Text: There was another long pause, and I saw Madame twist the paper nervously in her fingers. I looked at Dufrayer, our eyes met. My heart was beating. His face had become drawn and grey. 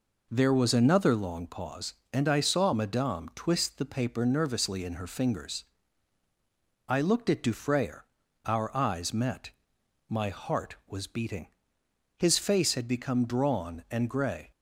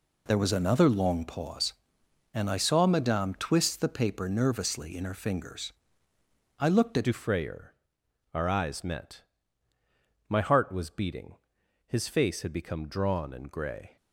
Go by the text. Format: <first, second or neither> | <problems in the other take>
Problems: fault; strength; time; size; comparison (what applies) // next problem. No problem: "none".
first | changes voice at "Dufrayer"; from 7.0 s on; 6.9 s long